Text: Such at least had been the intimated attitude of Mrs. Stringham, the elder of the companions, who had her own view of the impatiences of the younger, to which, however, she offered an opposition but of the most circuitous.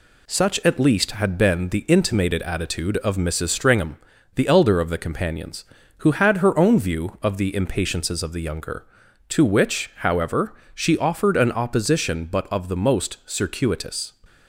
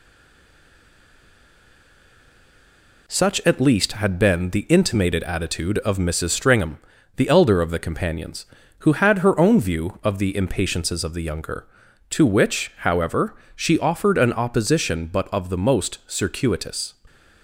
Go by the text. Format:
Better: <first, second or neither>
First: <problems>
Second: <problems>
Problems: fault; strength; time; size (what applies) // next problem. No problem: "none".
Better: first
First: none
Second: stays silent before the first word; strong; until 3.0 s; 3.0 s long